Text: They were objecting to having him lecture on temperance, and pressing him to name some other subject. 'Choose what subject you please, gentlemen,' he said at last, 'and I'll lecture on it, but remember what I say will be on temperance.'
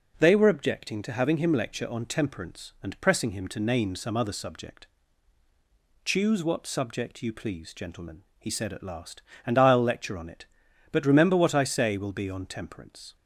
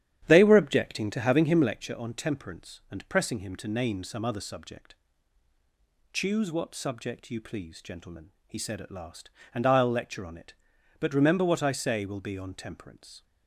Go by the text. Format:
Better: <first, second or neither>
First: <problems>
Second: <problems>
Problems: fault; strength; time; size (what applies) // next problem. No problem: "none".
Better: first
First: none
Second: starts louder than the rest; strong; until 1.7 s; 10 dB